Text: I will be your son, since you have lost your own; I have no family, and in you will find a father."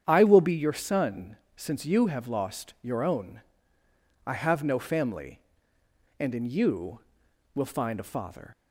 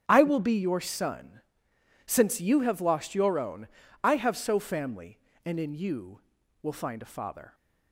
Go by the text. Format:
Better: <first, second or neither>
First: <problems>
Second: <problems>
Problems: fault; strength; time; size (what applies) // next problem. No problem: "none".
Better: first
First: starts louder than the rest; strong; until 1.0 s; 8.5 dB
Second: starts louder than the rest; strong; until 1.0 s; 8.5 dB // says "so" for "no"; at 4.3 s